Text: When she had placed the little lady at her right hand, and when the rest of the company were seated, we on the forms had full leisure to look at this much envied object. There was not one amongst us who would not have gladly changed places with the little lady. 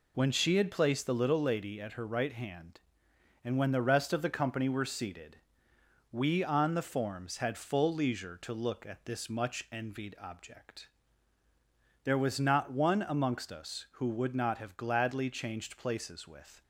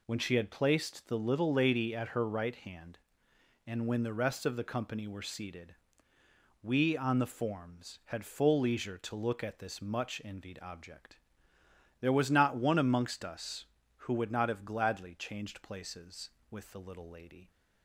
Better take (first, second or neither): second